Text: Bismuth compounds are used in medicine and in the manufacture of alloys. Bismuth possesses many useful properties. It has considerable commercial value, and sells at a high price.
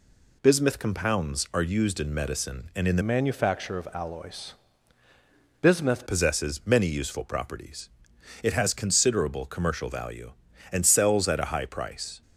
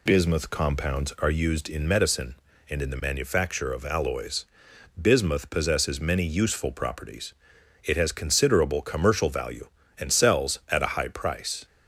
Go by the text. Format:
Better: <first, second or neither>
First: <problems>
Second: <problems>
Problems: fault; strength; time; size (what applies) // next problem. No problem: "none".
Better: second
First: changes voice from "manufacture" to "Bismuth"; from 3.0 to 6.0 s; 3.0 s long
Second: none